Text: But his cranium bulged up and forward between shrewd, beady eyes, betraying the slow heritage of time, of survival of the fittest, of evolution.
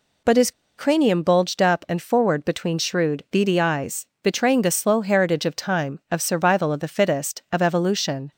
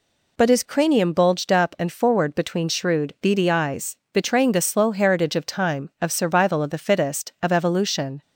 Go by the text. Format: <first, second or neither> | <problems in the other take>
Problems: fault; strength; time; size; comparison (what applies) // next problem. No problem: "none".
second | pauses between "his" and "cranium"; slight; at 0.5 s; 0.25 s long